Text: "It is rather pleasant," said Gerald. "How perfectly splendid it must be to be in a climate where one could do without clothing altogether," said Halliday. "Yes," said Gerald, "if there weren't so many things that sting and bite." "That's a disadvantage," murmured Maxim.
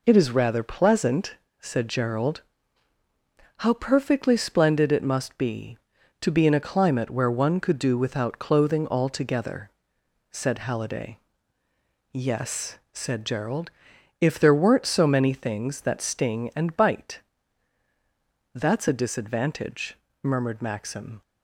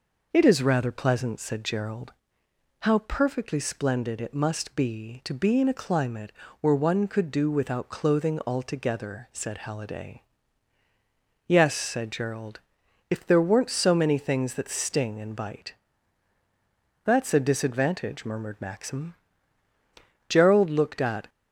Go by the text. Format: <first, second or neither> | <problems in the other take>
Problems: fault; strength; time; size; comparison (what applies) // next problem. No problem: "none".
first | pauses between "climate" and "where"; slight; at 6.3 s; 0.26 s long // goes on to say "Gerald looked at"; noticeable; from 20.2 s on; 1.0 s long